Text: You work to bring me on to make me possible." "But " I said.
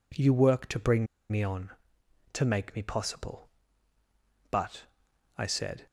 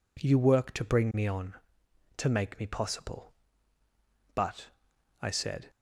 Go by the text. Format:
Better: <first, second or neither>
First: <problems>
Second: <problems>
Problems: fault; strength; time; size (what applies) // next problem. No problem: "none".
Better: second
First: pauses between "bring" and "me"; slight; at 1.0 s; 0.25 s long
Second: none